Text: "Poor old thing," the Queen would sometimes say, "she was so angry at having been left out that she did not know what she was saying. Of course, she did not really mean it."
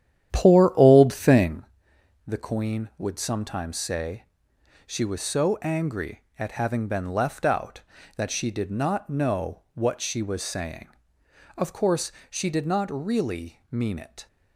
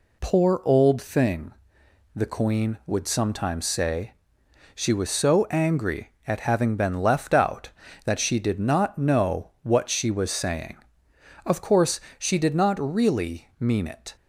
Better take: second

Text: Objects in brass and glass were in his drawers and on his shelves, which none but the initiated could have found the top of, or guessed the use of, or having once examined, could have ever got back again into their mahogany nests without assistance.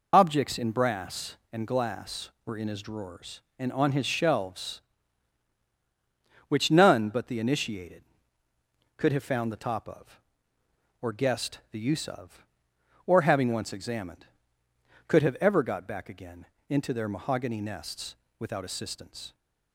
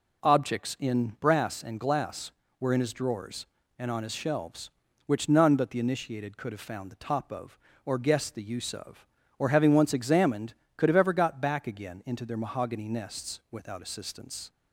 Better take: second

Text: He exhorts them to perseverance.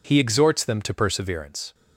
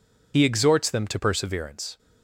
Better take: first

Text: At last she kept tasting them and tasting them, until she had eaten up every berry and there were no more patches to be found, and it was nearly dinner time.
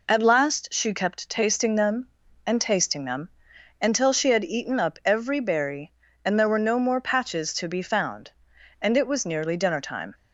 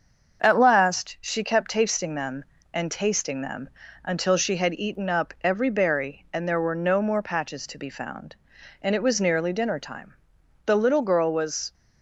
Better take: first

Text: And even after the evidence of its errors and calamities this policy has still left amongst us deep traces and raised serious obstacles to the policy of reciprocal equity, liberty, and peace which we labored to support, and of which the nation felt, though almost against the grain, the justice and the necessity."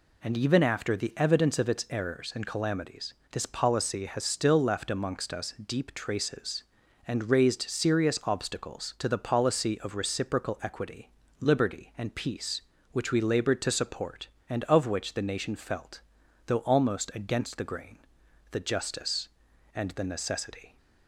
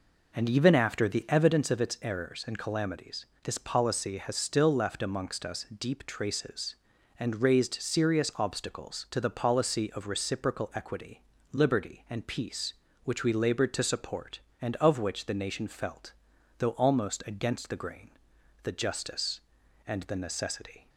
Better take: first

